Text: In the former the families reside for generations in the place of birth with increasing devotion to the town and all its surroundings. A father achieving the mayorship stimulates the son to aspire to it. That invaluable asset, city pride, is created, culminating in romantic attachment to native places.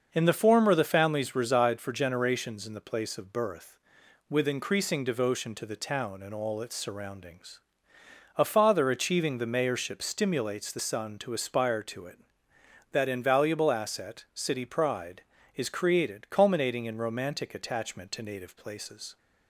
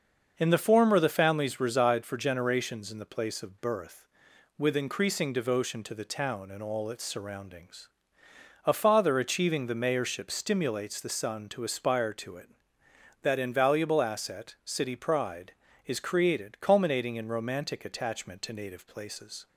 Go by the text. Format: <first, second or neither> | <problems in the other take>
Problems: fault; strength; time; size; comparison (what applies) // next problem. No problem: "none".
neither | starts louder than the rest; the same in both